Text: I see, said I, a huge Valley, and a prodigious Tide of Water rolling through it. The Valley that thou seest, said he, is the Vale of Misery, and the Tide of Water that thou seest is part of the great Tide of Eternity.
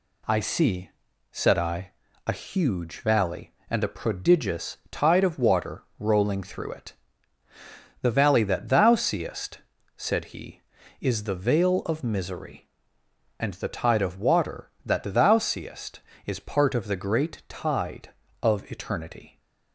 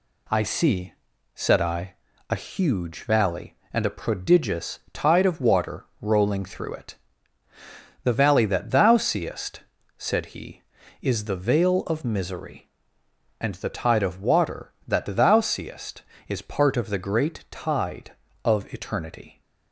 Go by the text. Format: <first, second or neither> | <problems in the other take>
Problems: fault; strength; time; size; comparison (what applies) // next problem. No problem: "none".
neither | pauses between "Water" and "rolling"; slight; the same in both